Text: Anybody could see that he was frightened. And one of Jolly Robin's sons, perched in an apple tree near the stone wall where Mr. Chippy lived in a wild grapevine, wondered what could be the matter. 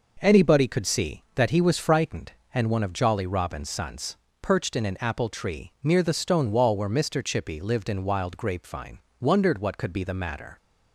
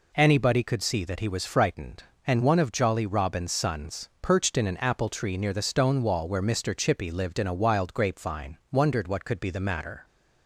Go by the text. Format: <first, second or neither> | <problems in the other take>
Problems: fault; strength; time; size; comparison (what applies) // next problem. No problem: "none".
second | skips "a"; at 8.0 s